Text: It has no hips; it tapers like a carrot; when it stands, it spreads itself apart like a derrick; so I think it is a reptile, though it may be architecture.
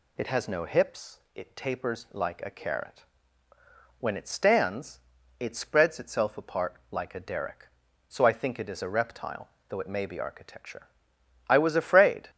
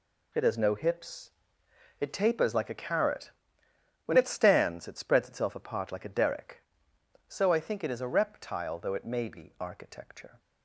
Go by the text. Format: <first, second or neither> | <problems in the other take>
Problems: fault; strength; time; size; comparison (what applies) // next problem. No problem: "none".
second | goes on to say "I was afraid"; noticeable; from 11.4 s on; 0.80 s long